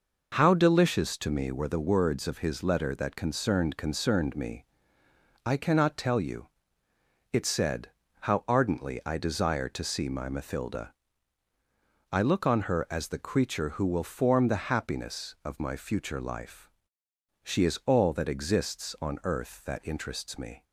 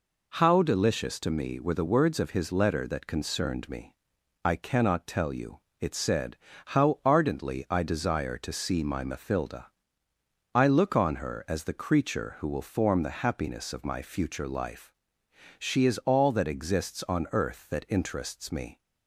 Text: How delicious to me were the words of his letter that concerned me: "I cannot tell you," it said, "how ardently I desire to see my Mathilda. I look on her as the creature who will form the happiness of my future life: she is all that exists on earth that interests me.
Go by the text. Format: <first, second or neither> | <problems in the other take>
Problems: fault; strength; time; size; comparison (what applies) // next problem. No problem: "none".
second | says "concerned" twice; at 3.7 s